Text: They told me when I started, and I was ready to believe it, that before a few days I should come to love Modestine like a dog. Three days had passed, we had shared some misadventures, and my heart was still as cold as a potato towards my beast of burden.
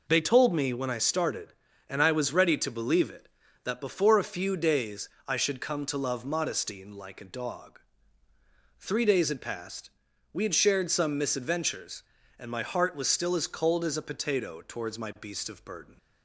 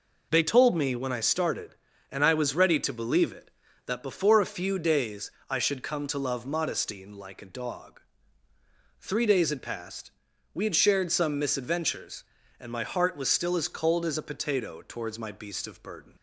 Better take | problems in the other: neither | pauses between "days" and "I"; slight; the same in both

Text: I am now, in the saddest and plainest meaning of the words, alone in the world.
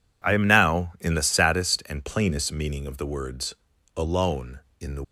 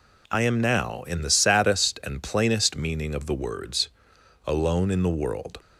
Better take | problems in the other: second | stops before "world"; at 5.0 s

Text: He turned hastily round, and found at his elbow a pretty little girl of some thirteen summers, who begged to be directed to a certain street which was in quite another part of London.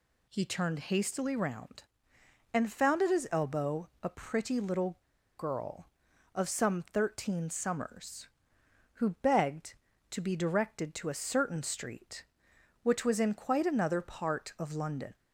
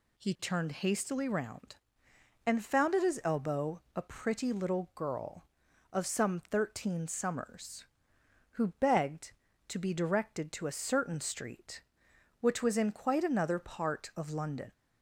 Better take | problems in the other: second | pauses between "elbow" and "a"; slight; at 3.8 s; 0.16 s long; slight in the second // pauses between "little" and "girl"; at 4.9 s; 0.39 s long

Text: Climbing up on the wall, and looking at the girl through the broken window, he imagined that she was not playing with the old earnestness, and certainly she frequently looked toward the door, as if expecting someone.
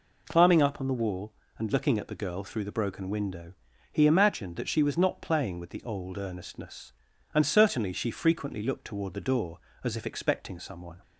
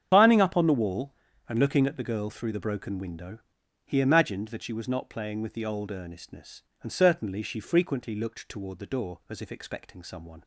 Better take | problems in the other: first | loses the start of "Climbing"; at 0.1 s; 65 ms // starts louder than the rest; strong; until 1.1 s; 8 dB

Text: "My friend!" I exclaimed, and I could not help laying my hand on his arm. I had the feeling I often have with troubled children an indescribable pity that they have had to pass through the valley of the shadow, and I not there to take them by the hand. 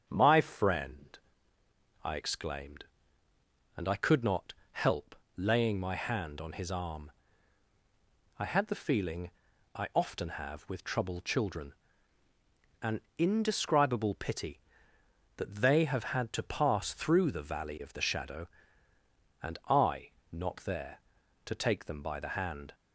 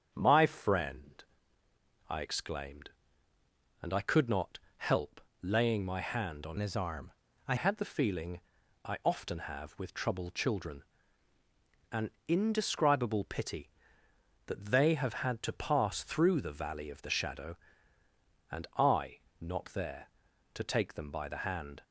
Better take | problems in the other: first | starts louder than the rest; strong; until 1.1 s; 7.5 dB; strong in the first // pauses between "not" and "help"; slight; at 4.5 s; 0.20 s long; slight in the first // pauses between "help" and "laying"; slight; at 5.2 s; 0.20 s long; slight in the first // changes voice from "his" to "I"; from 6.5 to 7.5 s; 1.0 s long // pauses between "feeling" and "I"; at 8.4 s; 0.42 s long; also in the first // pauses between "children" and "an"; at 10.8 s; 1.1 s long; also in the first // pauses between "an" and "indescribable"; slight; at 12.1 s; 0.16 s long; slight in the first // pauses between "I" and "not"; slight; at 19.2 s; 0.18 s long; slight in the first

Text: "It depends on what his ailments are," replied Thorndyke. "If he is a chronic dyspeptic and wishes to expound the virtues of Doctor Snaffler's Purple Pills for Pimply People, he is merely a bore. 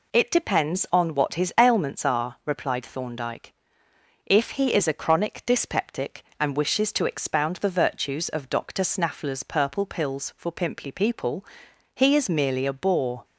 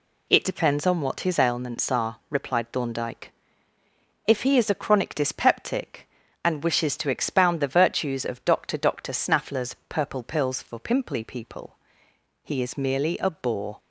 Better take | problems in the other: first | says "Doctor" twice; at 8.7 s

